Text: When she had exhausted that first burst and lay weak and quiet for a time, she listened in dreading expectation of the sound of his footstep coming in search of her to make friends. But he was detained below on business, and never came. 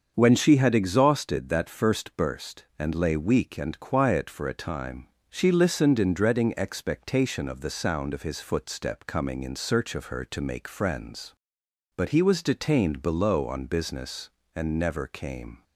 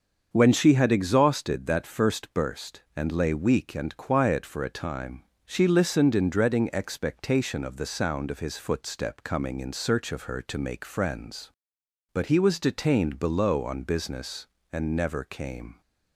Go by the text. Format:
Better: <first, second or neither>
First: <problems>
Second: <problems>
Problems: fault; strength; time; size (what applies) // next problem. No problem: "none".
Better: neither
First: starts louder than the rest; until 1.1 s; 6.5 dB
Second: starts louder than the rest; until 1.3 s; 6.5 dB